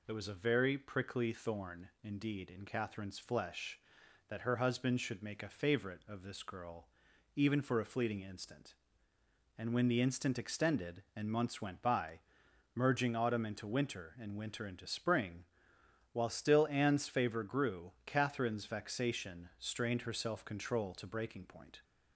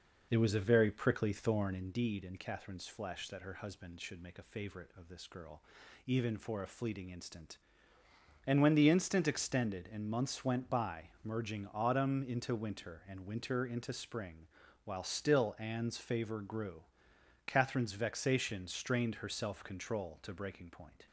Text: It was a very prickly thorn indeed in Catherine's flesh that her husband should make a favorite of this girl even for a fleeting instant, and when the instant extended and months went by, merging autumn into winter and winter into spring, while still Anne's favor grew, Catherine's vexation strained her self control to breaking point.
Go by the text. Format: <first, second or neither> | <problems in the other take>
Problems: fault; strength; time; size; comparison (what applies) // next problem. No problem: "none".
first | starts louder than the rest; noticeable; until 1.9 s; 5 dB // pauses between "girl" and "even"; at 5.6 s; 0.44 s long; noticeable in the first